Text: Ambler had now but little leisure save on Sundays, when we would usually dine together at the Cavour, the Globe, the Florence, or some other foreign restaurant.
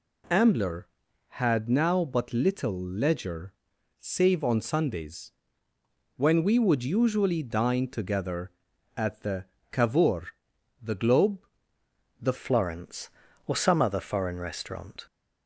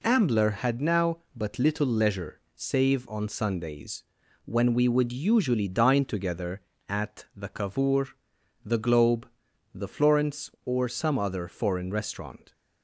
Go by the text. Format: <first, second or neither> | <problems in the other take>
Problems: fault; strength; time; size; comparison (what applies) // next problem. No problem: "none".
second | pauses between "leisure" and "save"; noticeable; at 3.5 s; 0.46 s long; slight in the second // pauses between "the" and "Cavour"; slight; at 9.4 s; 0.26 s long // changes voice at "Florence"; from 12.3 s on; 2.7 s long